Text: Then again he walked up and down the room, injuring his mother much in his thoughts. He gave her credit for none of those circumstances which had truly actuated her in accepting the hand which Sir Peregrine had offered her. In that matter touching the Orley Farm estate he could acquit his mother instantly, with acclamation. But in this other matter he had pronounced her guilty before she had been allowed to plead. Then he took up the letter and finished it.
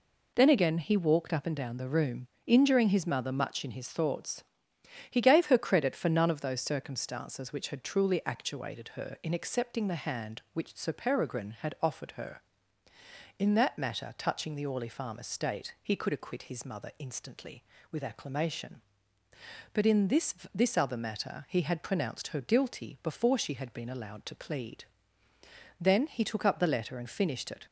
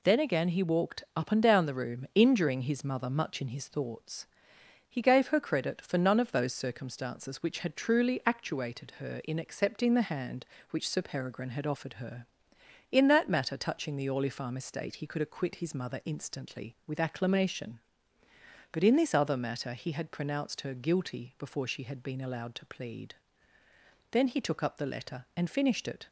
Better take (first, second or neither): second